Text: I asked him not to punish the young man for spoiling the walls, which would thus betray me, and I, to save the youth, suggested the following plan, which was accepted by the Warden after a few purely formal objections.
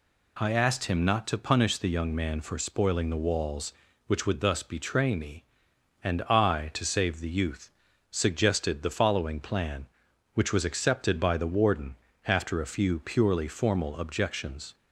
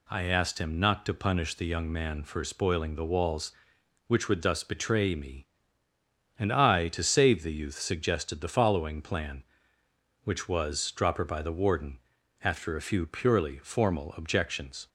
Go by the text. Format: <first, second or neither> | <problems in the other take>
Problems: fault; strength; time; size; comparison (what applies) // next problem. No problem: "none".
first | says "dropper" for "accepted"; at 10.9 s // pauses between "Warden" and "after"; at 11.9 s; 0.44 s long; slight in the first